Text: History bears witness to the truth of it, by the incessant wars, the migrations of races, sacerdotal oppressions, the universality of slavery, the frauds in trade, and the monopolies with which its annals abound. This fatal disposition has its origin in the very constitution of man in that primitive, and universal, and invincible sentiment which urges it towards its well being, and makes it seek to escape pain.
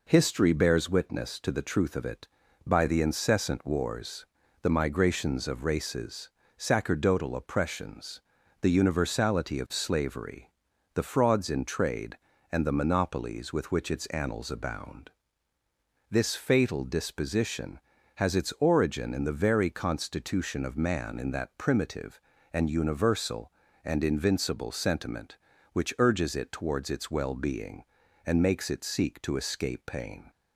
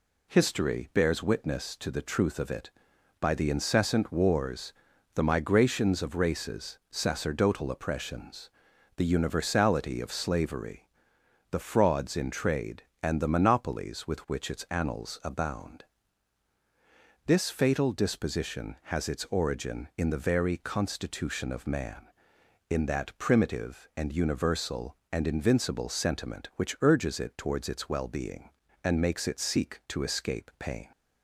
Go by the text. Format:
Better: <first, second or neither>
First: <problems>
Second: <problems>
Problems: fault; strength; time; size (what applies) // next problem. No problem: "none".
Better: neither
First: none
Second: none